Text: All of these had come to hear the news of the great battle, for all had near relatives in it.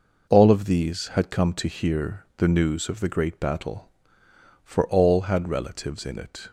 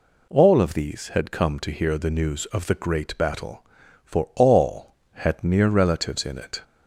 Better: second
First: skips "near"; at 5.4 s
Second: none

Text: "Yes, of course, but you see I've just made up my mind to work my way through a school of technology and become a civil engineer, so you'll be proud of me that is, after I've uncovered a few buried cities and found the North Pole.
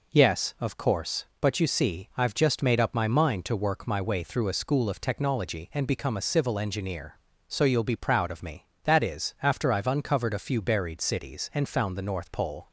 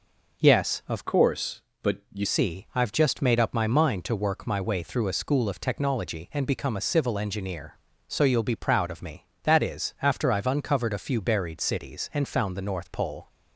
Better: first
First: none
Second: changes voice from "course" to "you"; from 1.0 to 2.2 s; 1.2 s long

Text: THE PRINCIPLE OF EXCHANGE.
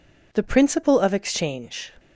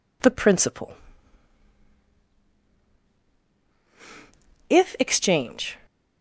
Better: first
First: none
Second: says "If" for "OF"; at 4.6 s

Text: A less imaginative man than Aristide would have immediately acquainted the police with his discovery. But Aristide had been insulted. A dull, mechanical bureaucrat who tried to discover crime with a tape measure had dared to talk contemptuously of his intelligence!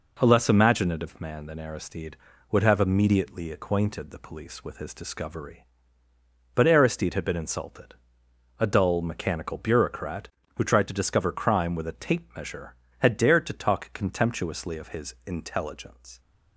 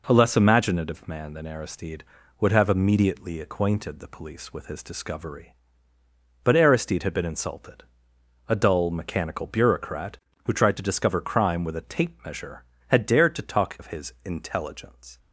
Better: first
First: none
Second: skips "contemptuously"; at 13.7 s

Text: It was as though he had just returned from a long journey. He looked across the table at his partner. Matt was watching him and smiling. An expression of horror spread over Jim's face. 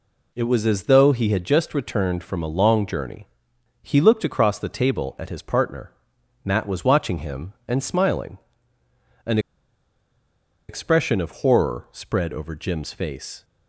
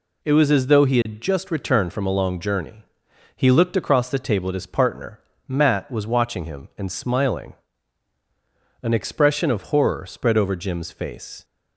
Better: second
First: pauses between "An" and "expression"; strong; at 9.3 s; 1.3 s long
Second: none

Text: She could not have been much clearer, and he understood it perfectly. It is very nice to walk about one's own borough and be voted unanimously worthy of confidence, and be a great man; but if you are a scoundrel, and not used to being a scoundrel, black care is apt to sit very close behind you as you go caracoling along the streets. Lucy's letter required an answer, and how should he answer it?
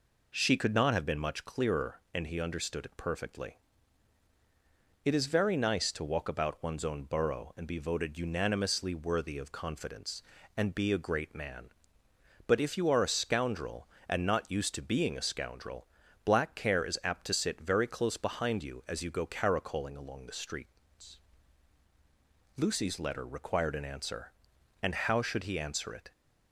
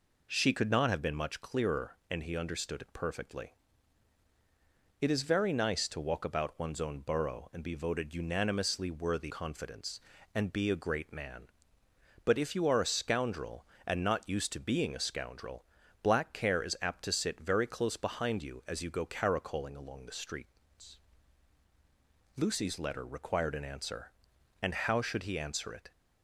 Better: first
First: none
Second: skips "of"; at 9.3 s

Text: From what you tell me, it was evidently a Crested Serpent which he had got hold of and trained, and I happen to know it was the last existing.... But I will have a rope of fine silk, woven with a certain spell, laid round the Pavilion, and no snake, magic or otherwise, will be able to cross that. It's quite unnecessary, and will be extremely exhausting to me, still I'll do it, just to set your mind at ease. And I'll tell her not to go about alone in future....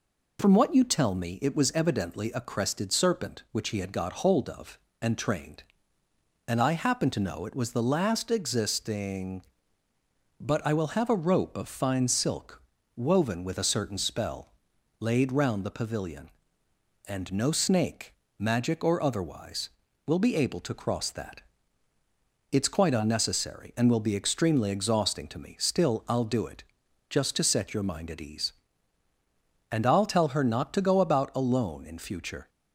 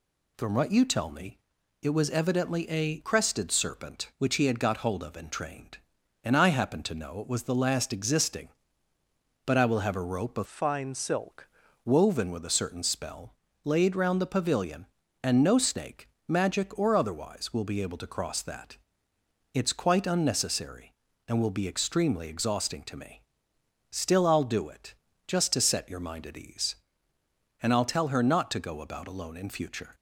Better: first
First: none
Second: changes voice from "fine" to "silk"; from 10.4 to 11.4 s; 1.0 s long

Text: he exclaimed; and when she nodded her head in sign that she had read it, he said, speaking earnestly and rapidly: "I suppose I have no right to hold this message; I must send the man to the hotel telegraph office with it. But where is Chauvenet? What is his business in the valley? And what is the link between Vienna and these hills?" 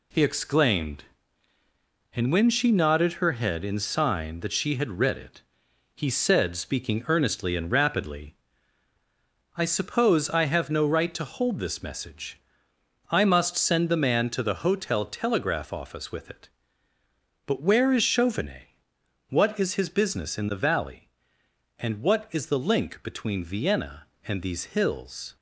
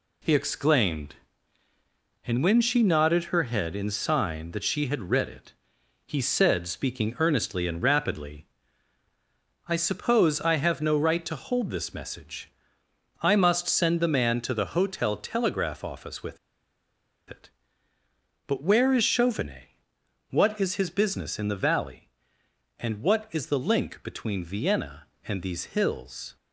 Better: first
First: none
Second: pauses between "with" and "it"; noticeable; at 16.3 s; 0.92 s long

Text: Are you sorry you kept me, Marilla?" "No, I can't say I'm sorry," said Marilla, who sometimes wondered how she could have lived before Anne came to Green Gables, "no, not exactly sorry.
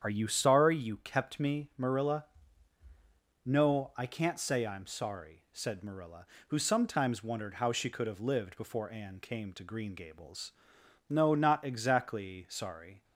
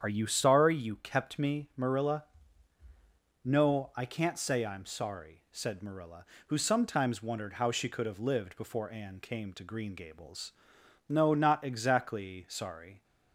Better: neither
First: starts louder than the rest; strong; until 1.0 s; 8.5 dB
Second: starts louder than the rest; strong; until 1.0 s; 8.5 dB

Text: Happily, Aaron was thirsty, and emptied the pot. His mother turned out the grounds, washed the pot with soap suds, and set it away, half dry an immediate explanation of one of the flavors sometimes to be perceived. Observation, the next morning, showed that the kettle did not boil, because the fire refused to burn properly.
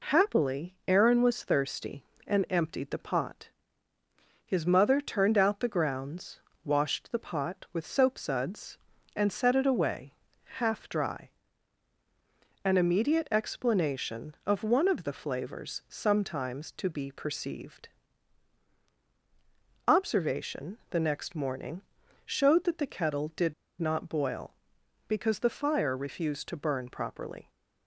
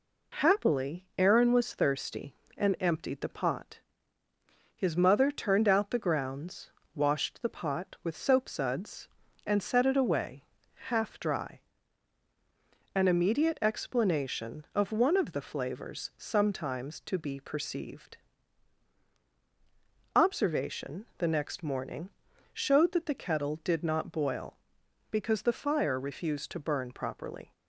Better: second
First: pauses between "dry" and "an"; strong; at 11.2 s; 1.3 s long // pauses between "did" and "not"; slight; at 23.5 s; 0.27 s long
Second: pauses between "dry" and "an"; strong; at 11.5 s; 1.3 s long

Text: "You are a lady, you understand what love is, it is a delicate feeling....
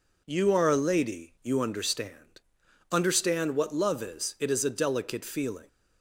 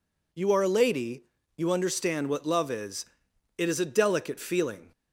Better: second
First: says "understand" twice; at 2.9 s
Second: none

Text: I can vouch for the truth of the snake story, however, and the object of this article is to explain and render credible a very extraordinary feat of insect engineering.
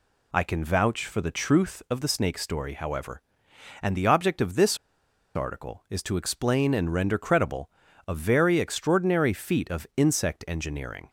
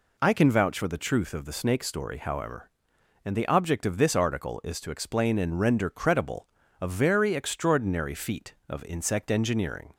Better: second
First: pauses between "this" and "article"; noticeable; at 4.7 s; 0.59 s long // pauses between "credible" and "a"; at 7.6 s; 0.38 s long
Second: pauses between "credible" and "a"; slight; at 6.4 s; 0.34 s long

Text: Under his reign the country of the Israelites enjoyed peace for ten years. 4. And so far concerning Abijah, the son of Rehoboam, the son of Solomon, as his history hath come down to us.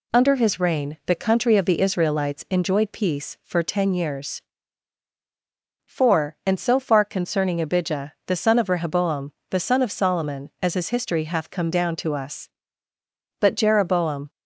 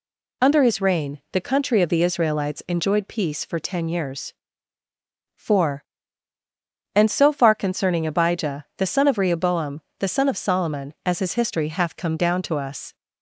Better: second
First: goes on to say "But Jeroboam"; noticeable; from 13.3 s on; 0.90 s long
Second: none

